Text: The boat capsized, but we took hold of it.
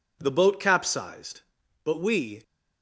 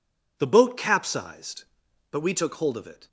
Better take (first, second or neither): second